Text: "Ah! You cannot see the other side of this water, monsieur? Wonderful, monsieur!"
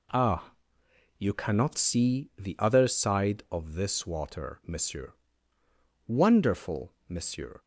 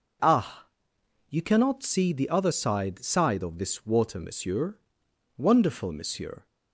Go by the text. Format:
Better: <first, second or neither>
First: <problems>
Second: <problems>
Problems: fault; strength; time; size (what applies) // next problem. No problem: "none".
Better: first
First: none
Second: says "side" twice; at 3.0 s